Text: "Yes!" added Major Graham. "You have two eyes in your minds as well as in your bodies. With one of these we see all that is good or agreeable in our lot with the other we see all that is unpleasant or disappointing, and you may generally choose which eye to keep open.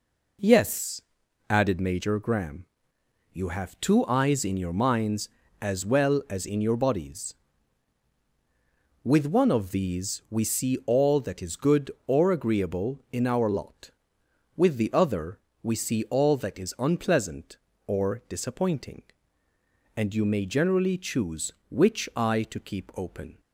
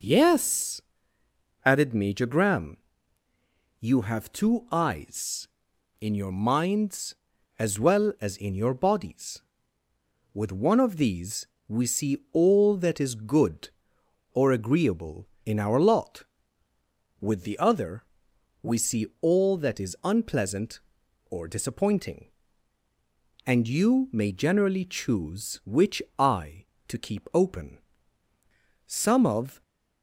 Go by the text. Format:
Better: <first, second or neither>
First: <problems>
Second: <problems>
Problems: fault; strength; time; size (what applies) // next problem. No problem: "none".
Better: first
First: pauses between "other" and "we"; slight; at 15.3 s; 0.24 s long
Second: pauses between "these" and "we"; slight; at 11.4 s; 0.22 s long // pauses between "other" and "we"; noticeable; at 18.0 s; 0.60 s long // pauses between "see" and "all"; slight; at 19.0 s; 0.16 s long // pauses between "which" and "eye"; slight; at 26.0 s; 0.16 s long // goes on to say "Some of"; noticeable; from 28.8 s on; 0.74 s long